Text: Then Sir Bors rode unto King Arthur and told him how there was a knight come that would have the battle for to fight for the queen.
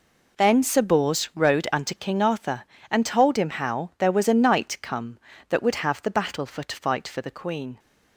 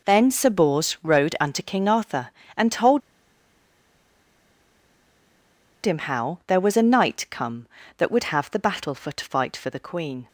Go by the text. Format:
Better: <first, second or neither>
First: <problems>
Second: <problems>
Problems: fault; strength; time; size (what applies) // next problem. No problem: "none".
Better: first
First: none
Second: pauses between "told" and "him"; strong; at 3.0 s; 2.8 s long